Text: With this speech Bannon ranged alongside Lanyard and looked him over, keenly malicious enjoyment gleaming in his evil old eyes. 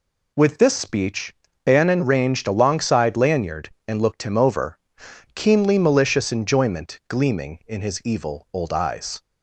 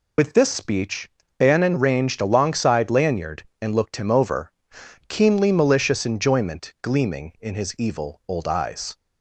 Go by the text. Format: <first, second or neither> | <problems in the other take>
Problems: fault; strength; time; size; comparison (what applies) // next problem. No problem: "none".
first | loses the start of "With"; at 0.1 s; 80 ms // pauses between "speech" and "Bannon"; slight; at 1.1 s; 0.26 s long; slight in the first